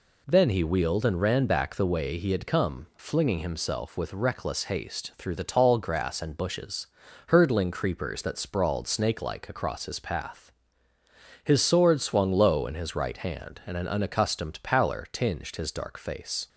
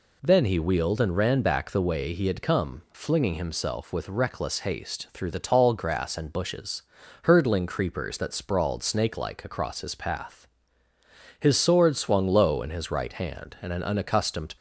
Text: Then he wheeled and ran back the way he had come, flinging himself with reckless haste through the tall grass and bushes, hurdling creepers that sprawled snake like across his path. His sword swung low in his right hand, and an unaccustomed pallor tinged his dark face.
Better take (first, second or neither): first